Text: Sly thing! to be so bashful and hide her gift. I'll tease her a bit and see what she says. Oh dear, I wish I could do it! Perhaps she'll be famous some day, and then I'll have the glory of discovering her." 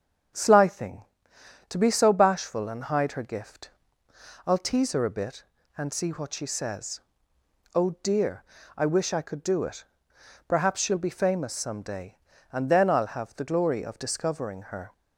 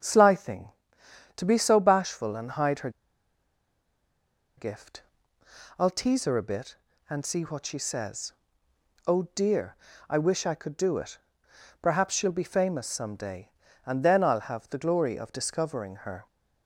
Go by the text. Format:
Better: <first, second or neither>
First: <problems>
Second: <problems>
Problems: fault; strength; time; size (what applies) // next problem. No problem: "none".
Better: first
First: starts louder than the rest; strong; until 1.9 s; 7.5 dB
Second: starts louder than the rest; strong; until 1.6 s; 7.5 dB // pauses between "her" and "gift"; strong; at 2.8 s; 1.6 s long